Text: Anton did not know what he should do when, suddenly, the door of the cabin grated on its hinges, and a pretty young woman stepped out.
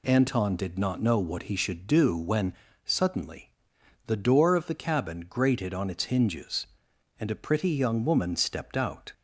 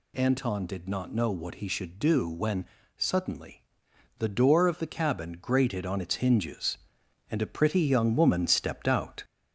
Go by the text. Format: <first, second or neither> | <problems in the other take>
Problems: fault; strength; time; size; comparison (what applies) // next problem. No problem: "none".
first | gets louder; slight; throughout; 3 dB